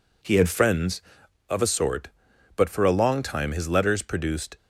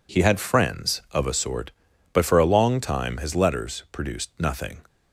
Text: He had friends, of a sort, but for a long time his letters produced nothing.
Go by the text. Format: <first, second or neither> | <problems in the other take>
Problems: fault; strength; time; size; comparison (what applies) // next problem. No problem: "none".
second | stops before "nothing"; at 4.5 s